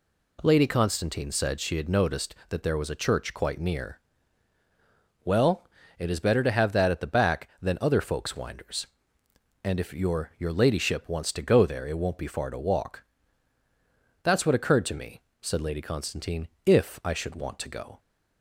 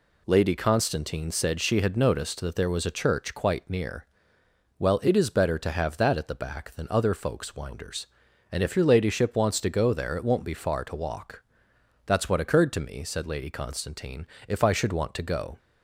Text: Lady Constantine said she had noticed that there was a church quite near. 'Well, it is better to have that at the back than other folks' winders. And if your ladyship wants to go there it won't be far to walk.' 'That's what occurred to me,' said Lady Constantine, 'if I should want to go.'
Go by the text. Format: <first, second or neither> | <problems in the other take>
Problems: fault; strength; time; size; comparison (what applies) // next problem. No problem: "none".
second | says "your" twice; at 10.3 s